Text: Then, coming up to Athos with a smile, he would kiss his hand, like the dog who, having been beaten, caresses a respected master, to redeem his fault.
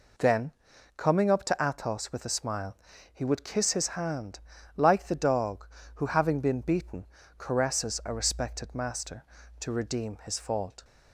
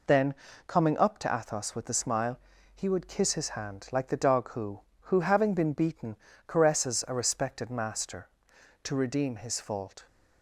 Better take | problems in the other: first | says "who" twice; at 5.0 s

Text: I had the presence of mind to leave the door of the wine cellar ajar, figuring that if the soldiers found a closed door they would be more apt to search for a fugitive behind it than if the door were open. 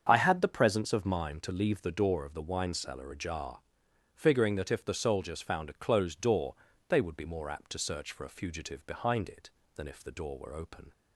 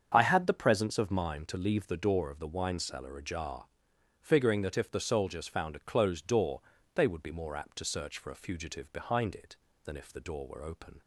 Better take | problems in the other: neither | starts louder than the rest; the same in both // pauses between "door" and "they"; slight; the same in both

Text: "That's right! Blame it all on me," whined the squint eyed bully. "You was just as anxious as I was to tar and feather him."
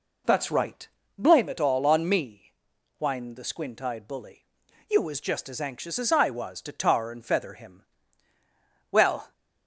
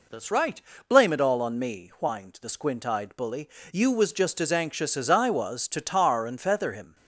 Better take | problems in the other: second | goes on to say "Well"; slight; from 8.9 s on; 0.40 s long

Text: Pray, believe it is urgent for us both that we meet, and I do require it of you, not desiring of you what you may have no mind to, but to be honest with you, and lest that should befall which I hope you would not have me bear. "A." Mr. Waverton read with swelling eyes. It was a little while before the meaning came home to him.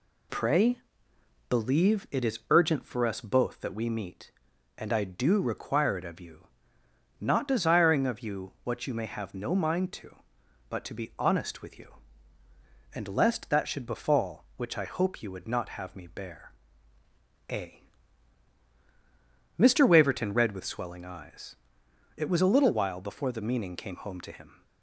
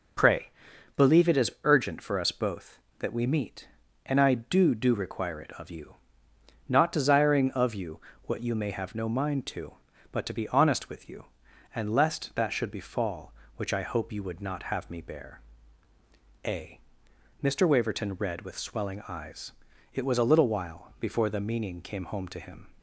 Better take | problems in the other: first | says "do" twice; at 4.7 s // pauses between "you" and "what"; slight; at 8.0 s; 0.24 s long

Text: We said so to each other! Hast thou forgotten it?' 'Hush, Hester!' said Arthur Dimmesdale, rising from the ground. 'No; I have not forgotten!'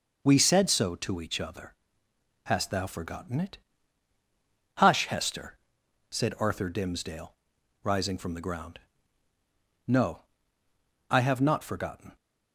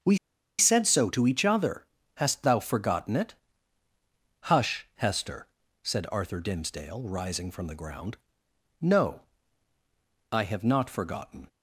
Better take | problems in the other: first | starts louder than the rest; until 1.4 s; 7 dB // pauses between "We" and "said"; at 0.1 s; 0.41 s long

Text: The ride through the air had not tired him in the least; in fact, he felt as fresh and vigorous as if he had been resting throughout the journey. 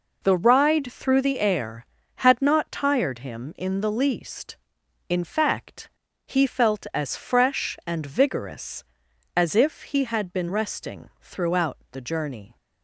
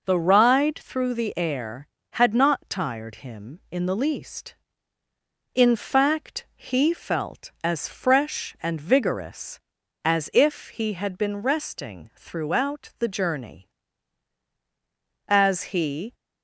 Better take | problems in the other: first | goes on to say "As he"; noticeable; from 15.2 s on; 0.86 s long

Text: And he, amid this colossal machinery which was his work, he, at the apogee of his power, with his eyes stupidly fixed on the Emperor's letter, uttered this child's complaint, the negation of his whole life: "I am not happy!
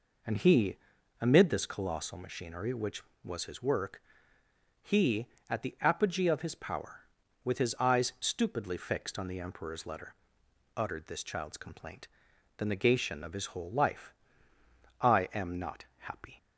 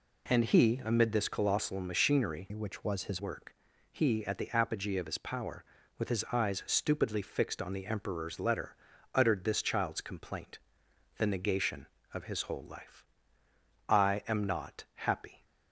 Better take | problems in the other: first | changes voice from "which" to "his"; from 2.5 to 3.1 s; 0.6 s long

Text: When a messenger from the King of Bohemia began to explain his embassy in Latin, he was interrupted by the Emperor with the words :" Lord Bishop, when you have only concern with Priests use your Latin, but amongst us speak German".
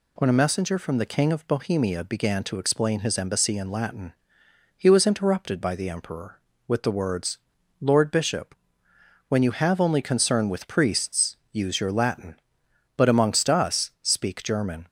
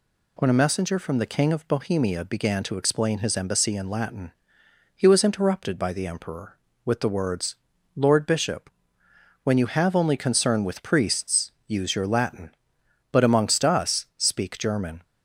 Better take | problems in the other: neither | pauses between "Priests" and "use"; slight; the same in both

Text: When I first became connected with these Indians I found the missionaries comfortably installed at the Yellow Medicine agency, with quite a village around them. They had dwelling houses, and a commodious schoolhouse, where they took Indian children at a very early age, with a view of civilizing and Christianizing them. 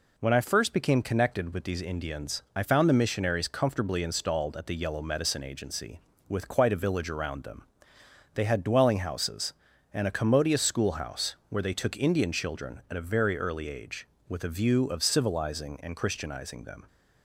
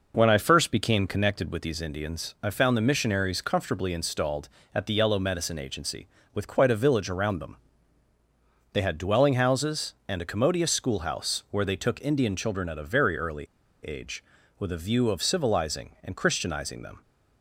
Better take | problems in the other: first | pauses between "early" and "age"; at 13.4 s; 0.44 s long

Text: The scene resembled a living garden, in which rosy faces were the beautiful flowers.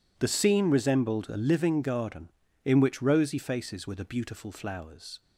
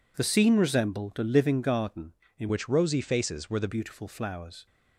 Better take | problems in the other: first | changes voice from "which" to "the"; from 2.4 to 3.6 s; 1.2 s long

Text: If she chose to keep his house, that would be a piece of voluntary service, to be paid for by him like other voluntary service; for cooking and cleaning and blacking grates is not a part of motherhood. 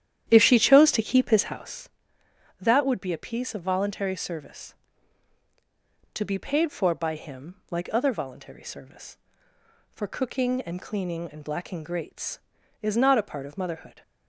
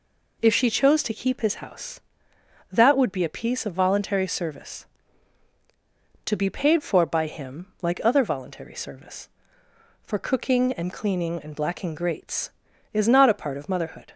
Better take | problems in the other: second | starts louder than the rest; strong; until 1.8 s; 10.5 dB

